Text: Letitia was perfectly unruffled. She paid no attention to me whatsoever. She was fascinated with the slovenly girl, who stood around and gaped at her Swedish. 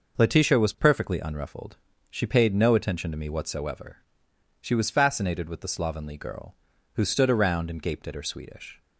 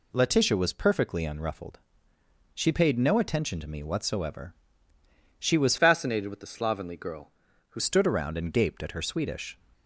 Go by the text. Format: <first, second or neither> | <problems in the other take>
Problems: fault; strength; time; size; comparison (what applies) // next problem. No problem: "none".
first | changes voice from "fascinated" to "who"; from 5.7 to 7.7 s; 2.0 s long